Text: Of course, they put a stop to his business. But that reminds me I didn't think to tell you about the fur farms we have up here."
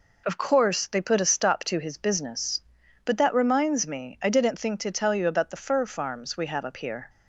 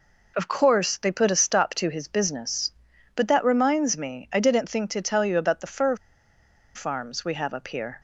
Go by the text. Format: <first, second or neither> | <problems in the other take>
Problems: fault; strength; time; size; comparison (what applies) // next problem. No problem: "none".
first | pauses between "fur" and "farms"; noticeable; at 5.9 s; 0.80 s long